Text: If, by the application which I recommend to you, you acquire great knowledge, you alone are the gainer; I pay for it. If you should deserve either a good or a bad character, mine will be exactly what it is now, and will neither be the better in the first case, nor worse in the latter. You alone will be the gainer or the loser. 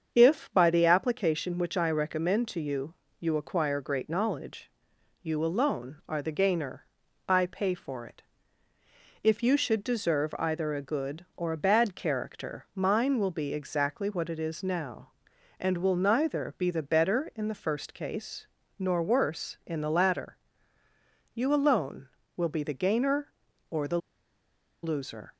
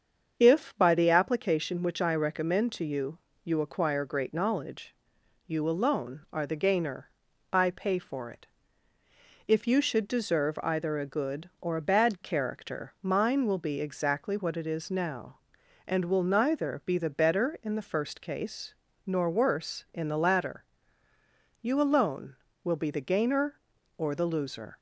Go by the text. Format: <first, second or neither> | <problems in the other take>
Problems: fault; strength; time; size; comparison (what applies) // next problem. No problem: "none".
second | starts louder than the rest; strong; until 1.1 s; 7 dB; strong in the second // pauses between "the" and "loser"; noticeable; at 23.9 s; 0.85 s long